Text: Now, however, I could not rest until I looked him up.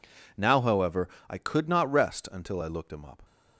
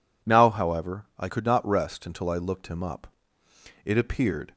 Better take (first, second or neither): first